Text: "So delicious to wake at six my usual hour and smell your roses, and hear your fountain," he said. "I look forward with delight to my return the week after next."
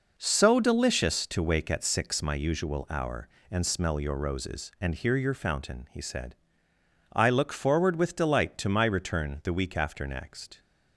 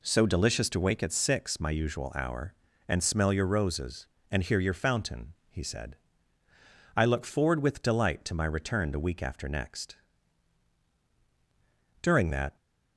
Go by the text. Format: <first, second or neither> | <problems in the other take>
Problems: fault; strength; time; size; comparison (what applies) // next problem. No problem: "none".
first | goes on to say "During that"; from 12.0 s on; 0.54 s long